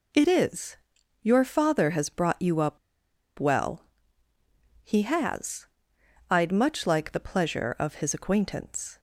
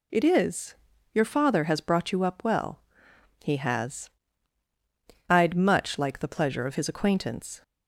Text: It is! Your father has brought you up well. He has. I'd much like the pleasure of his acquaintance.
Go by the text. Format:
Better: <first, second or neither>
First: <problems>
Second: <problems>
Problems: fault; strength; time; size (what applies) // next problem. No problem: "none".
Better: second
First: pauses between "up" and "well"; noticeable; at 2.7 s; 0.61 s long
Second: none